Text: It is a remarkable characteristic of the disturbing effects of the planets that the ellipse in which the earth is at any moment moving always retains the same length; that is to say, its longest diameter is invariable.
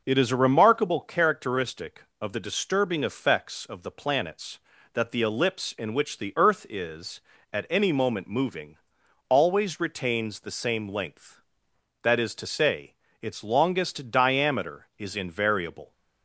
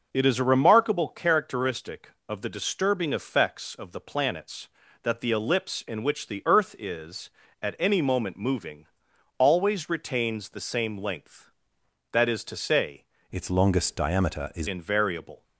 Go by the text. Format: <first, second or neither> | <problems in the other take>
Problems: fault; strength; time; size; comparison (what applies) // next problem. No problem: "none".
first | pauses between "moving" and "always"; noticeable; at 8.8 s; 0.52 s long; noticeable in the first // changes voice from "its" to "is"; from 13.3 to 14.6 s; 1.3 s long